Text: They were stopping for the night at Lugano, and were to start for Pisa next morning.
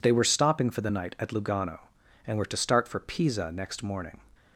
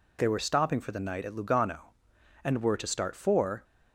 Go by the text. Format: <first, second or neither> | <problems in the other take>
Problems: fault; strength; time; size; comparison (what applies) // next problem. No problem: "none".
first | stops before "Pisa next morning"; at 3.6 s